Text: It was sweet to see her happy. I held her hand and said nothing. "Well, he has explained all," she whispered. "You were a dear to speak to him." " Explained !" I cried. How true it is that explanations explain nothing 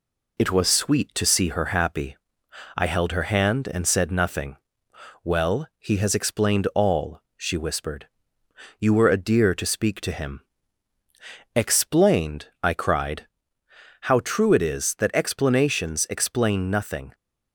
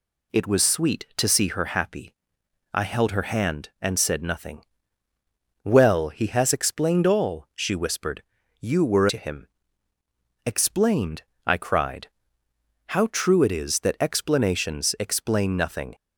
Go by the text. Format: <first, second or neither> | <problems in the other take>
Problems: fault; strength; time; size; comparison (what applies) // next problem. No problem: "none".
first | skips "a dear to speak"; at 9.0 s